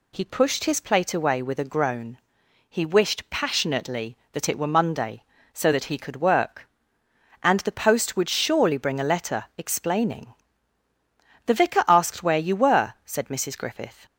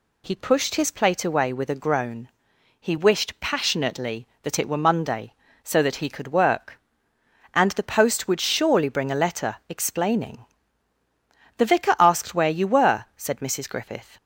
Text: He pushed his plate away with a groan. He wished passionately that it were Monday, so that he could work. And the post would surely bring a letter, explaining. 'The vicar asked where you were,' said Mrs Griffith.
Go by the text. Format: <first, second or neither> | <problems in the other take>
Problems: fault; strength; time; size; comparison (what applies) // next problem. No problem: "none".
neither | none